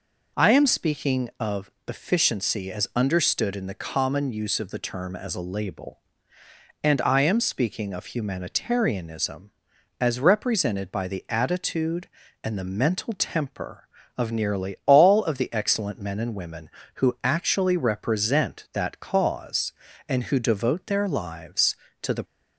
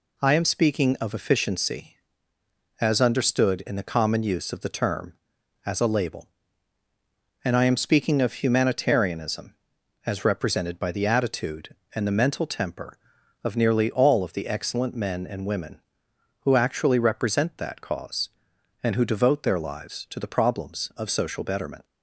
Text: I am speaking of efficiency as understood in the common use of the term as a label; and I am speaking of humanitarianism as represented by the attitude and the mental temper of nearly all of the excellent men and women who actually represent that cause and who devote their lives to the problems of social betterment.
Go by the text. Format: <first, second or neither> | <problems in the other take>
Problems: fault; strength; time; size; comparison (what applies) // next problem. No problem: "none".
second | pauses between "of" and "efficiency"; slight; at 1.6 s; 0.18 s long // stops before "problems of social betterment"; at 22.2 s